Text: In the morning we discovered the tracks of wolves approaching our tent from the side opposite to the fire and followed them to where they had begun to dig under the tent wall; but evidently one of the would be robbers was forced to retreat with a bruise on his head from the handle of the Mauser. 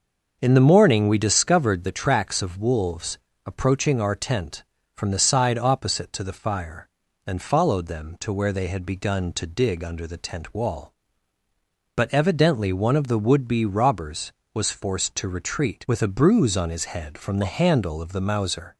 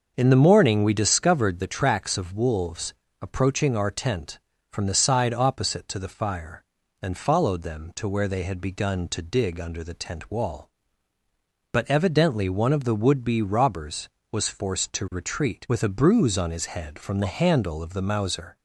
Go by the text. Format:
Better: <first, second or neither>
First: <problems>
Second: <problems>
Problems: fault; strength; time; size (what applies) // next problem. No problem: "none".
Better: neither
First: starts louder than the rest; until 1.4 s; 6.5 dB // pauses between "wolves" and "approaching"; slight; at 3.1 s; 0.26 s long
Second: starts louder than the rest; until 1.1 s; 6.5 dB // pauses between "wolves" and "approaching"; slight; at 2.9 s; 0.26 s long